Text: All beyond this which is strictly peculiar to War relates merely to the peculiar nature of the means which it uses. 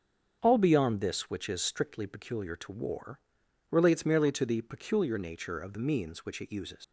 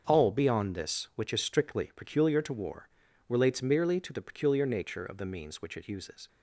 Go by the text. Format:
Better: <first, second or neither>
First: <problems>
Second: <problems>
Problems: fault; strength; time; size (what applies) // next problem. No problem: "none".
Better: second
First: starts louder than the rest; strong; until 1.4 s; 7 dB // pauses between "War" and "relates"; noticeable; at 3.1 s; 0.52 s long // leaves "uses" unfinished; at 6.8 s; 105 ms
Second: starts louder than the rest; until 1.0 s; 6.5 dB // pauses between "War" and "relates"; at 2.8 s; 0.38 s long